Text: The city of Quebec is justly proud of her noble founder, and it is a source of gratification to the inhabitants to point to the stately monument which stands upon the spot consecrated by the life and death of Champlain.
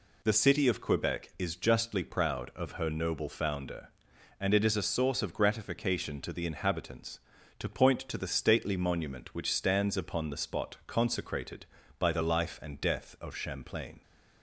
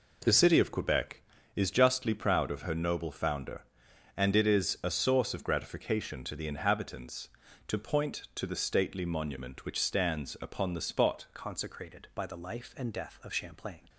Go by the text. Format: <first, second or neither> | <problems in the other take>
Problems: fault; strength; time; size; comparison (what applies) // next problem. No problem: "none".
first | changes voice at "consecrated"; from 11.3 s on; 2.5 s long